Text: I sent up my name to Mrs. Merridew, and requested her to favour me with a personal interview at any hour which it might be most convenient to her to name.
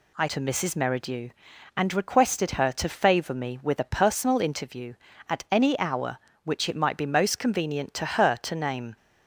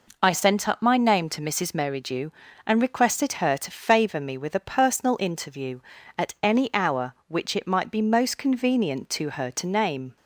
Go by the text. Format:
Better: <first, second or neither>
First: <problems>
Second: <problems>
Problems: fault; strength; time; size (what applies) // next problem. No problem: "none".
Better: second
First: skips "sent up my name"; at 0.2 s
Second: none